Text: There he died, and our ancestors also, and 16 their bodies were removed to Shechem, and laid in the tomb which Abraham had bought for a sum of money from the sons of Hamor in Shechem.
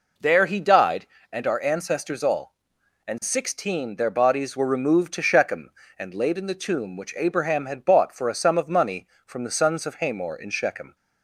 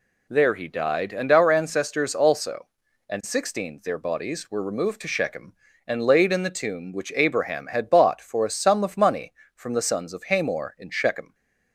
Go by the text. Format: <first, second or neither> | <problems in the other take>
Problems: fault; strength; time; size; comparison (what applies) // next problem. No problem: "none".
second | says "all" for "also"; at 2.2 s